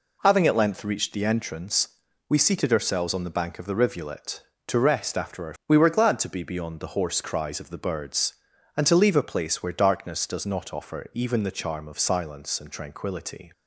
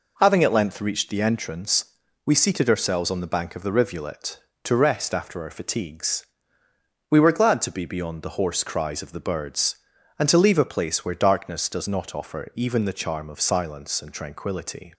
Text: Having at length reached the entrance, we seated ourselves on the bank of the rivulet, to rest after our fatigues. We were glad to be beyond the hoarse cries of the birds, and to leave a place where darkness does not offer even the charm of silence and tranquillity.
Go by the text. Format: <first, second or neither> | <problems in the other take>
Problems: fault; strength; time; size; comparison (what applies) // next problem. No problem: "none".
second | skips "fatigues"; at 5.6 s